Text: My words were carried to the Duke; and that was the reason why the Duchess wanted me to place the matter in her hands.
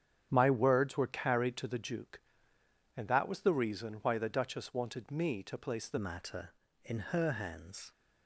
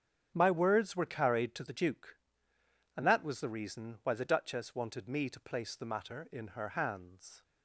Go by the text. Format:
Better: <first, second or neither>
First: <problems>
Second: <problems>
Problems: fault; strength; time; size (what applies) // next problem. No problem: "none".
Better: second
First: starts louder than the rest; strong; until 1.3 s; 9.5 dB // changes voice at "matter"; from 5.9 s on; 2.0 s long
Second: starts louder than the rest; strong; until 1.3 s; 8.5 dB